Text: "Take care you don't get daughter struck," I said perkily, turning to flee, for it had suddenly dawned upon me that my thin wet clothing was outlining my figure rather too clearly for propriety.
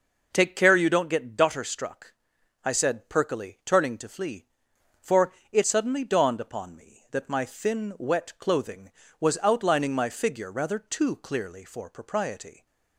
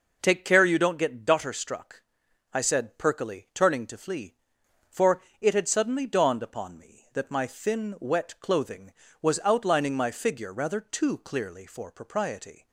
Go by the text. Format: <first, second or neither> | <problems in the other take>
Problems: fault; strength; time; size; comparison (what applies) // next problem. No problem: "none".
second | pauses between "for" and "it"; slight; at 5.3 s; 0.18 s long; slight in the second // skips "had"; at 5.6 s